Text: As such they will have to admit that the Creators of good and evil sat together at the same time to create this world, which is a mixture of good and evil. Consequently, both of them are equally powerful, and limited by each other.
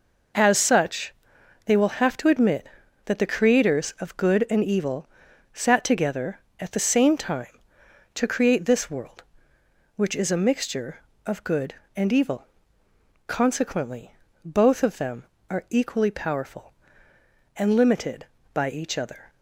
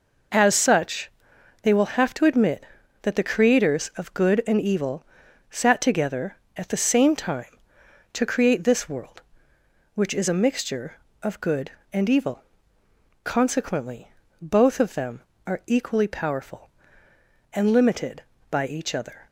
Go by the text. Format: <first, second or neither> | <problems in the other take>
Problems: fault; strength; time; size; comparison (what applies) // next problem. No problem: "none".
neither | pauses between "such" and "they"; noticeable; the same in both // pauses between "evil" and "sat"; noticeable; the same in both